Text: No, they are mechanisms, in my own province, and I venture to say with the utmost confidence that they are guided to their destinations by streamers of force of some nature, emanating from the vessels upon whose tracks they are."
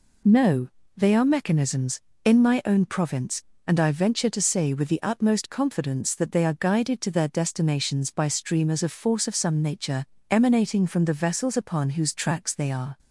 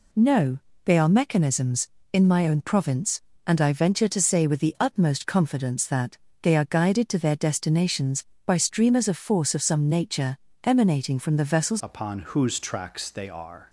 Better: first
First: none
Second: pauses between "that" and "they"; slight; at 6.1 s; 0.24 s long // changes voice at "upon"; from 11.8 s on; 1.8 s long

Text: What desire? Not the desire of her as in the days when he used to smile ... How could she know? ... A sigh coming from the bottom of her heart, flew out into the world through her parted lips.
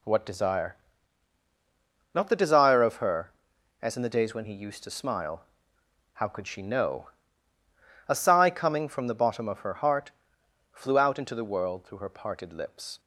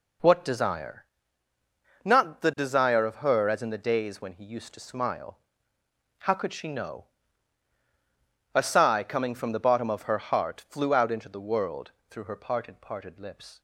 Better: first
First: none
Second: pauses between "world" and "through"; slight; at 11.9 s; 0.18 s long // says "parted" twice; at 12.8 s

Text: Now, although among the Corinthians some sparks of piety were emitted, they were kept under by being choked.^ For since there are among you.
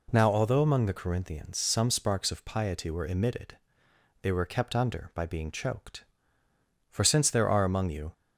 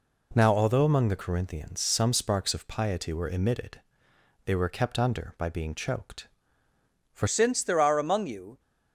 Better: first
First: none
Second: changes voice at "since"; from 7.2 s on; 1.3 s long

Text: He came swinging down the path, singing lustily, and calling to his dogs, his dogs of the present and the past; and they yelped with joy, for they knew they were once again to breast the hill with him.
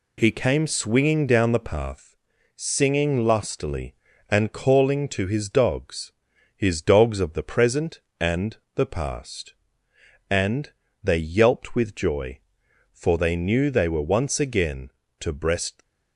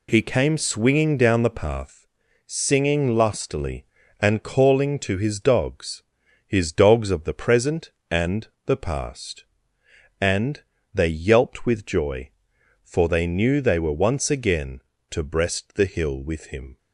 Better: second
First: pauses between "and" and "the"; slight; at 8.5 s; 0.18 s long // pauses between "and" and "they"; slight; at 10.7 s; 0.28 s long // stops before "the hill with him"; at 15.8 s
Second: pauses between "and" and "the"; slight; at 8.4 s; 0.18 s long // pauses between "and" and "they"; slight; at 10.6 s; 0.28 s long

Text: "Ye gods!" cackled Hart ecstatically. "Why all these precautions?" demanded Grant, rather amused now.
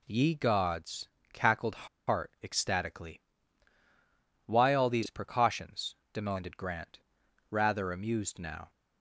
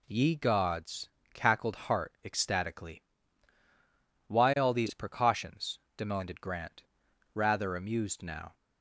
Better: second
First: pauses between "cackled" and "Hart"; slight; at 1.8 s; 0.21 s long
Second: none

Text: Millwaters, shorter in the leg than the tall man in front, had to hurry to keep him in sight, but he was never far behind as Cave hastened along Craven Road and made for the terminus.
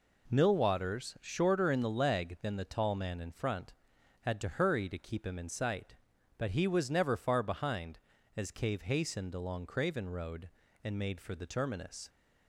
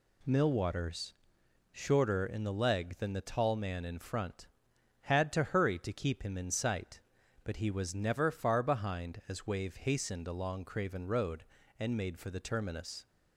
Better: first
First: none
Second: says "Wave" for "Cave"; at 9.4 s

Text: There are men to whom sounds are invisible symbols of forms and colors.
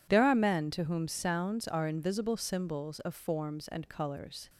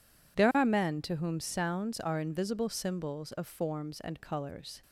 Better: neither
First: none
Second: none

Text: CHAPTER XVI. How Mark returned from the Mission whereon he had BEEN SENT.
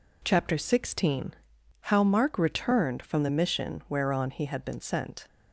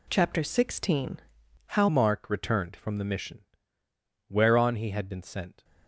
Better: first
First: none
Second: changes voice at "Mark"; from 1.8 s on; 3.8 s long // pauses between "Mission" and "whereon"; noticeable; at 3.4 s; 0.86 s long

